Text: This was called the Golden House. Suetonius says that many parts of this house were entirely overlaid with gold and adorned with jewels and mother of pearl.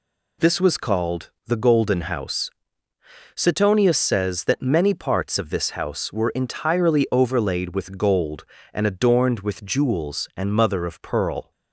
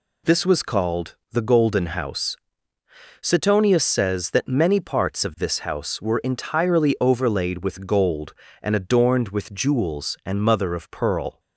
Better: neither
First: pauses between "called" and "the"; slight; at 1.3 s; 0.16 s long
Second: pauses between "called" and "the"; slight; at 1.1 s; 0.16 s long

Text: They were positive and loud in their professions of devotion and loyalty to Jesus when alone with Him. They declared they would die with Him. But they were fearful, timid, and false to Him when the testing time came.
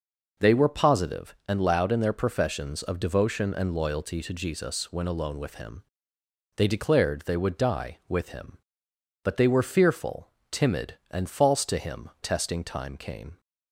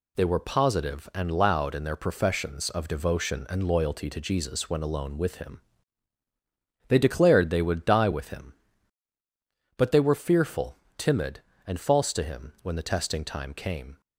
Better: second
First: skips "when the"; at 12.1 s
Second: none

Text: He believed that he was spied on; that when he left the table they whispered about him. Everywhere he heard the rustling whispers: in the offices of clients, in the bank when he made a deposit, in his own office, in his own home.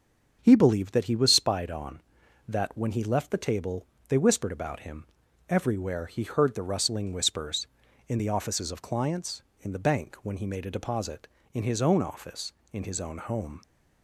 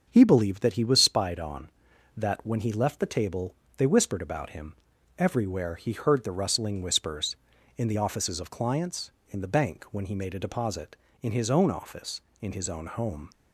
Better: neither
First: starts louder than the rest; until 1.4 s; 7 dB // pauses between "table" and "they"; slight; at 3.8 s; 0.22 s long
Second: starts louder than the rest; until 1.1 s; 7 dB // pauses between "table" and "they"; slight; at 3.5 s; 0.22 s long

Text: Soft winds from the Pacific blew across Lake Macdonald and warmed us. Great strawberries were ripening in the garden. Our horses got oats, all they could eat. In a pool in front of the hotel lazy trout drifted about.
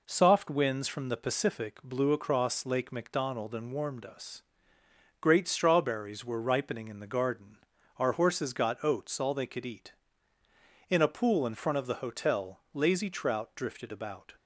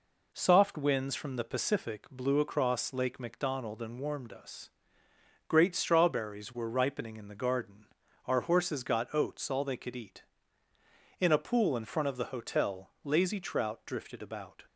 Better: neither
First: none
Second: none

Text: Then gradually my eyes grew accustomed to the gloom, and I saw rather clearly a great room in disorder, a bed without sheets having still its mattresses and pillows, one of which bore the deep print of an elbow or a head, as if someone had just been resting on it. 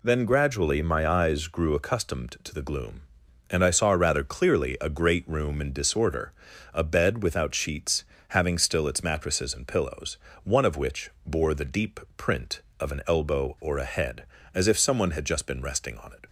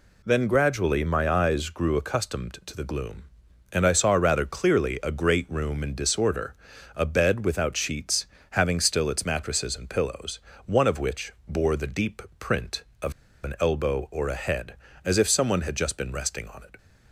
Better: first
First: pauses between "sheets" and "having"; slight; at 8.0 s; 0.24 s long // pauses between "which" and "bore"; slight; at 11.1 s; 0.16 s long // pauses between "deep" and "print"; slight; at 12.0 s; 0.16 s long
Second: pauses between "sheets" and "having"; slight; at 8.2 s; 0.24 s long // pauses between "which" and "bore"; slight; at 11.3 s; 0.16 s long // pauses between "deep" and "print"; slight; at 12.2 s; 0.16 s long // pauses between "of" and "an"; slight; at 13.1 s; 0.32 s long

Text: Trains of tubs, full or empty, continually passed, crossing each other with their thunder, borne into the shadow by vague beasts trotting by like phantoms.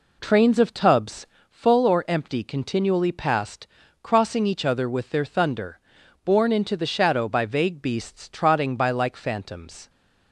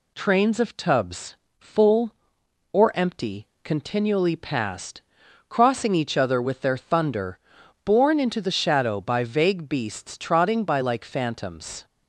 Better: second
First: starts louder than the rest; slight; until 1.5 s; 3.5 dB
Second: none

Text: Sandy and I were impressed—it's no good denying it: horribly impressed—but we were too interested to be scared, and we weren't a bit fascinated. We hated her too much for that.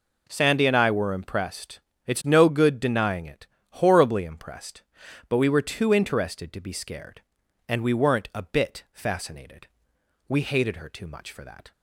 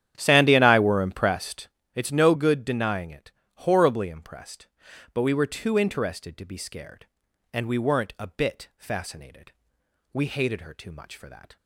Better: first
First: none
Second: starts louder than the rest; strong; until 1.7 s; 10 dB

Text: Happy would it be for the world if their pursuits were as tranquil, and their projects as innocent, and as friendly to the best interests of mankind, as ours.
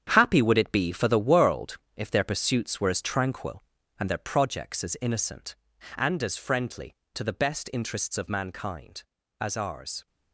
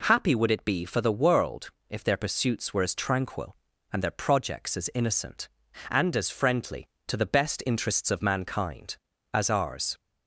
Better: second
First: gets quieter; strong; throughout; 10 dB // pauses between "world" and "if"; slight; at 1.7 s; 0.18 s long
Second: pauses between "world" and "if"; slight; at 1.6 s; 0.18 s long

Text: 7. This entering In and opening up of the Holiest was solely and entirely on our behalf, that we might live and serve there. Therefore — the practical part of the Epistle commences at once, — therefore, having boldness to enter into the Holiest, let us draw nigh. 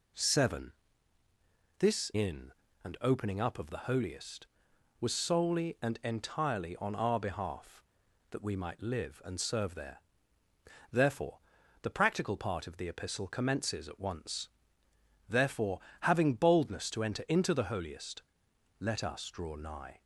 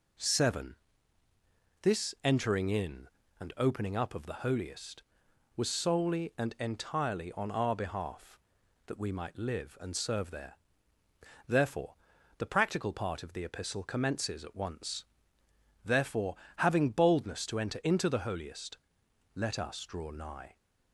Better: second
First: skips "entering"; at 2.1 s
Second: none

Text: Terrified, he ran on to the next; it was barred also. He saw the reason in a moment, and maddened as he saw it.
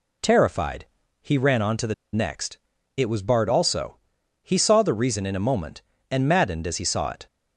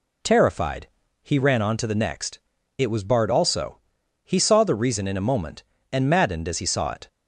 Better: second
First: pauses between "the" and "next"; slight; at 1.9 s; 0.19 s long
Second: none

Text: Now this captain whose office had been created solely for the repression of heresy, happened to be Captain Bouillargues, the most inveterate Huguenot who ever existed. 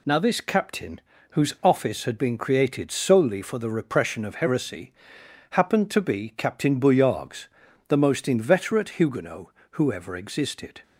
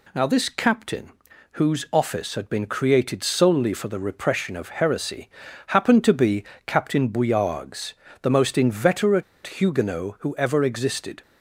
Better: first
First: pauses between "captain" and "whose"; slight; at 0.9 s; 0.32 s long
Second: pauses between "captain" and "whose"; at 1.1 s; 0.40 s long // pauses between "be" and "Captain"; slight; at 6.4 s; 0.24 s long // pauses between "inveterate" and "Huguenot"; slight; at 9.2 s; 0.22 s long

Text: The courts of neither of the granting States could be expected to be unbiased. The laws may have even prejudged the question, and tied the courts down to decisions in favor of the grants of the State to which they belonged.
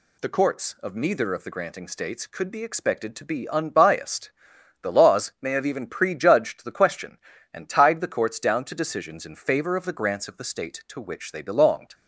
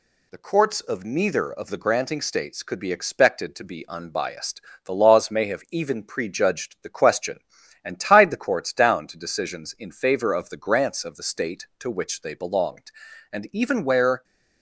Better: first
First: none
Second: goes on to say "And even where"; noticeable; from 13.3 s on; 0.92 s long

